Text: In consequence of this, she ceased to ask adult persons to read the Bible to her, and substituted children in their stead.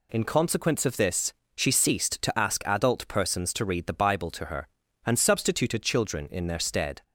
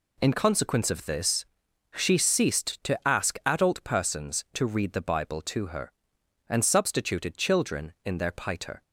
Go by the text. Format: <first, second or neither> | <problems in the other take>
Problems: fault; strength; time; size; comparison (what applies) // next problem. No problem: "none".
first | says "piter" for "stead"; at 8.3 s